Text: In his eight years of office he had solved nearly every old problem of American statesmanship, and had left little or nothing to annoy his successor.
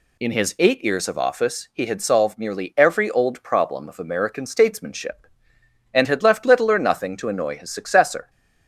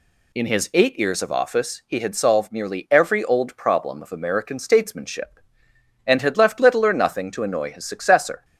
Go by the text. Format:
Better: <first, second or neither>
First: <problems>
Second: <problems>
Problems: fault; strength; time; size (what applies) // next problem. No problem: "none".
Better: neither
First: none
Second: none